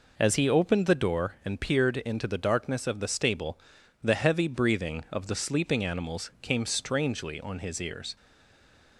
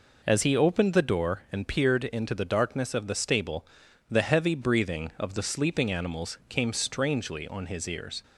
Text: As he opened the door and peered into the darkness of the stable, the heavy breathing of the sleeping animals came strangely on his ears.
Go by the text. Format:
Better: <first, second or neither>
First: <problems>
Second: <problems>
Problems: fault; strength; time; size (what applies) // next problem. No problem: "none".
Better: second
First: stays silent after the last word; slight; from 8.1 s on; 0.8 s long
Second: none